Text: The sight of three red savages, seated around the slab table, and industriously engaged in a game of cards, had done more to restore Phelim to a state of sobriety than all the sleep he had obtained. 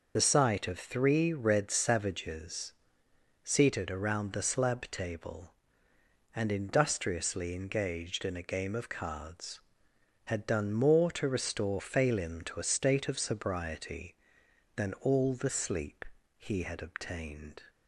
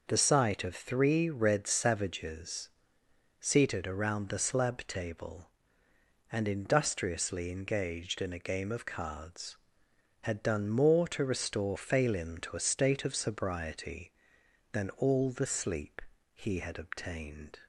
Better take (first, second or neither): second